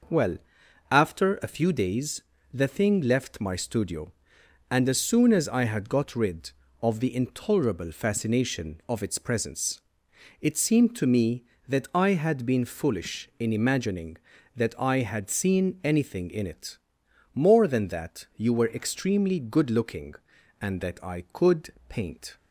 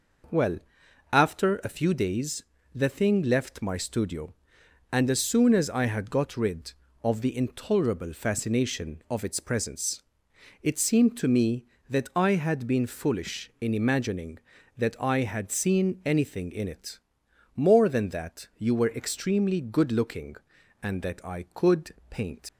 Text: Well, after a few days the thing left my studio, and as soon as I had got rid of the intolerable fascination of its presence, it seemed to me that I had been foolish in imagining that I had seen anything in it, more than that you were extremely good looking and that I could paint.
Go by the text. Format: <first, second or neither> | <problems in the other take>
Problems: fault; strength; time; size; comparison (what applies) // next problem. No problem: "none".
first | pauses between "days" and "the"; slight; at 2.4 s; 0.30 s long; slight in the first // pauses between "could" and "paint"; slight; at 21.9 s; 0.18 s long; slight in the first // leaves "paint" unfinished; at 22.4 s; 80 ms